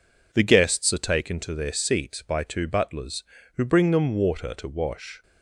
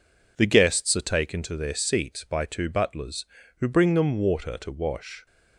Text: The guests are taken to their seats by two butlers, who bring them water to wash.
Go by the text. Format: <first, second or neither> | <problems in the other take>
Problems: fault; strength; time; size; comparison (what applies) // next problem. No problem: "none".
neither | none